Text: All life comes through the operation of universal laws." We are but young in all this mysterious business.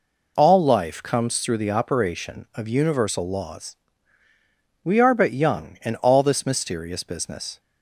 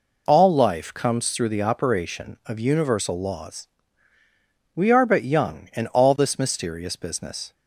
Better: neither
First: none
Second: none

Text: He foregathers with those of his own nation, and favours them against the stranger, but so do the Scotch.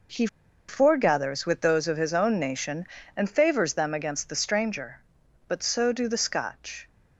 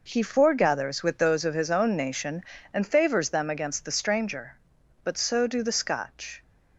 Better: second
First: pauses between "He" and "foregathers"; at 0.2 s; 0.42 s long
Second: none

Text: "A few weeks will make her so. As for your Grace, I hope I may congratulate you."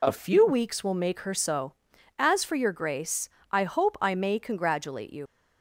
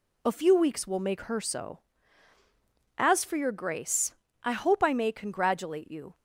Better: second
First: leaves "you" unfinished; at 5.2 s; 85 ms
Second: none

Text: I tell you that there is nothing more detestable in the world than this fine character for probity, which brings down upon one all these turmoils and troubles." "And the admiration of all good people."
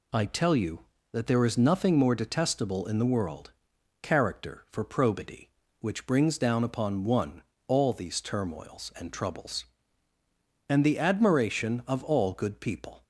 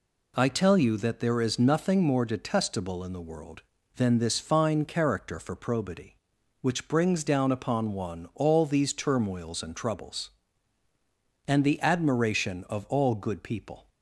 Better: second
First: skips "than this fine"; at 3.7 s // pauses between "one" and "all"; slight; at 7.4 s; 0.24 s long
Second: none

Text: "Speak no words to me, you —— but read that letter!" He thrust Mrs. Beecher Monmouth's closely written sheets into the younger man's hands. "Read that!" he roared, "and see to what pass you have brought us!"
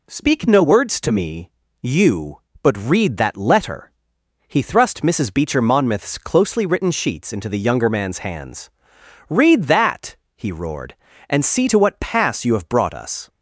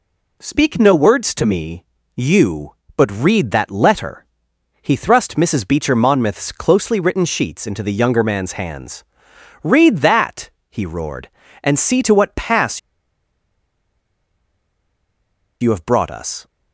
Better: first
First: none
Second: pauses between "pass" and "you"; strong; at 12.7 s; 2.8 s long

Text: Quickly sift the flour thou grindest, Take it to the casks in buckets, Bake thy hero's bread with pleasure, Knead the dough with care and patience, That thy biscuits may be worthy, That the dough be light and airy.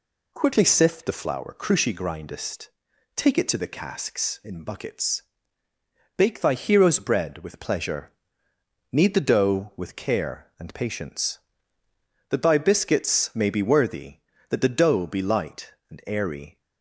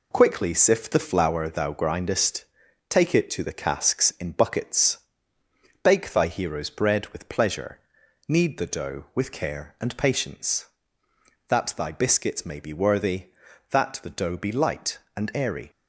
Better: second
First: says "cruci" for "thou"; at 1.5 s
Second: none

